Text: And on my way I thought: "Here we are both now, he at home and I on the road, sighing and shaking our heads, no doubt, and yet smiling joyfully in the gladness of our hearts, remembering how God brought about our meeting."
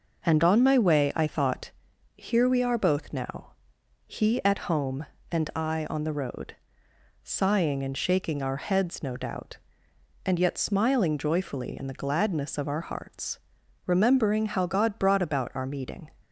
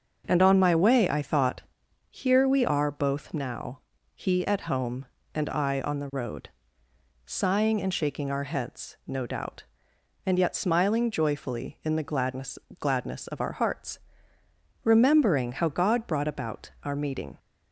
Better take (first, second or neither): first